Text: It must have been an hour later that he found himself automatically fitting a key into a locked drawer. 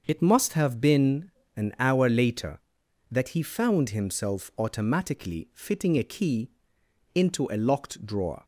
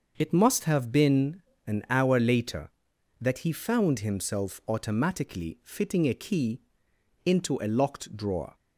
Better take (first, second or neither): neither